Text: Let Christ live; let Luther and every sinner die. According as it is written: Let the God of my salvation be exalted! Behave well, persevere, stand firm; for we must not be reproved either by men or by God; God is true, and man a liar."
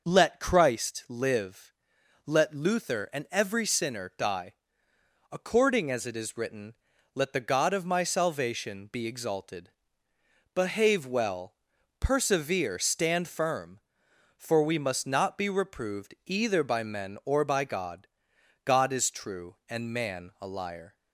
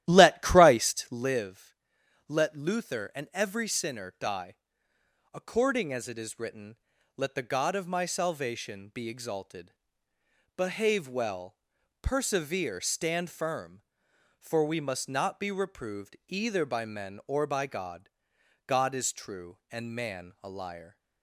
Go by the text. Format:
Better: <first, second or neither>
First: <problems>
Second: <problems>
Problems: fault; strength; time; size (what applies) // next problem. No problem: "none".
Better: first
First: none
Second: starts louder than the rest; strong; until 1.3 s; 13.5 dB